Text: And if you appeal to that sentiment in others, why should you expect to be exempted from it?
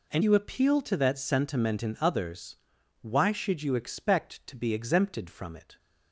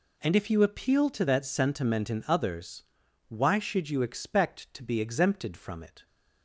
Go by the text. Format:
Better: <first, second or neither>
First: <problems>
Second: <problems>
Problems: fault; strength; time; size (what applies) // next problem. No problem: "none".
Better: second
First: skips "if"; at 0.2 s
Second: none